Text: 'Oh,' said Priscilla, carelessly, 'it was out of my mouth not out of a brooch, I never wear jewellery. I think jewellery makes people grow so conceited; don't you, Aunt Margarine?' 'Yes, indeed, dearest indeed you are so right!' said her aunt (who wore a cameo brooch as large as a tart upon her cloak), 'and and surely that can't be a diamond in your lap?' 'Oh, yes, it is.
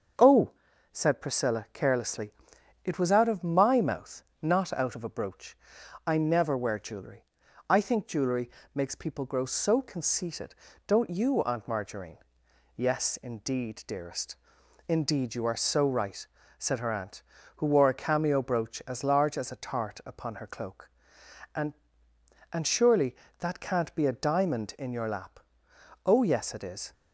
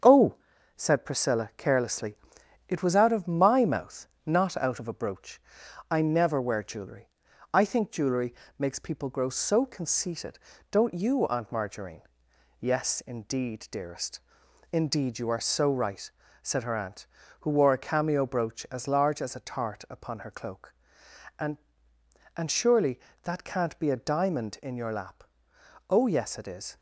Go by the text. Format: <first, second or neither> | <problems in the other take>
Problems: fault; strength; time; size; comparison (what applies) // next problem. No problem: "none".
first | gets quieter; noticeable; throughout; 4 dB // starts louder than the rest; strong; until 1.4 s; 7.5 dB; also in the first // pauses between "mouth" and "not"; slight; at 4.0 s; 0.18 s long; slight in the first // pauses between "jewellery" and "makes"; slight; at 8.3 s; 0.24 s long; slight in the first // pauses between "dearest" and "indeed"; noticeable; at 14.2 s; 0.50 s long; noticeable in the first